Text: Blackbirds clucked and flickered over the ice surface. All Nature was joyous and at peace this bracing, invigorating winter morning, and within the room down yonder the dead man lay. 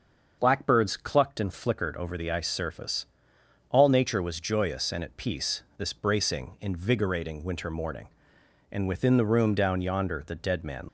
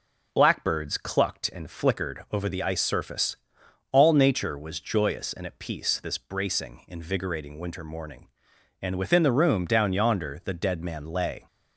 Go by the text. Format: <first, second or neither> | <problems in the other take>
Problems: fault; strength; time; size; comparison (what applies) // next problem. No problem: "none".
second | starts louder than the rest; until 1.4 s; 6.5 dB // stops before "lay"; at 10.8 s